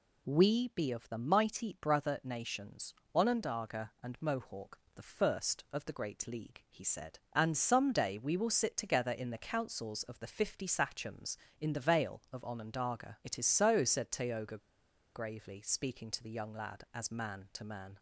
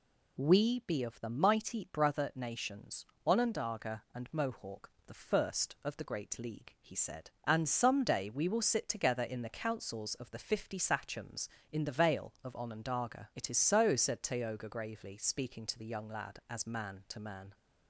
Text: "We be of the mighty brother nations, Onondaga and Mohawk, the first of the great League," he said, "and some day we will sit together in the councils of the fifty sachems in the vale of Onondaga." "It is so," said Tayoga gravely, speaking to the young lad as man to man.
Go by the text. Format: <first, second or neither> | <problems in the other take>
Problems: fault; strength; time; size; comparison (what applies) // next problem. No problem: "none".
second | pauses between "Tayoga" and "gravely"; noticeable; at 14.5 s; 0.56 s long